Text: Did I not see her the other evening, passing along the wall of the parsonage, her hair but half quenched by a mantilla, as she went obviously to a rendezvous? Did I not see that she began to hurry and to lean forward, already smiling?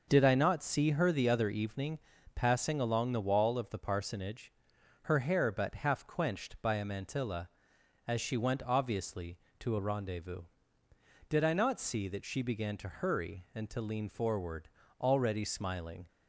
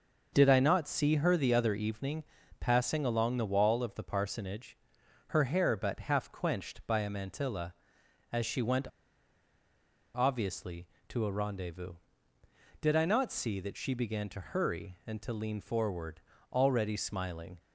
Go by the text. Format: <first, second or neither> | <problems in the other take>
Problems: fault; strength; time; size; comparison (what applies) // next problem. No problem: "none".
first | pauses between "went" and "obviously"; strong; at 8.8 s; 1.2 s long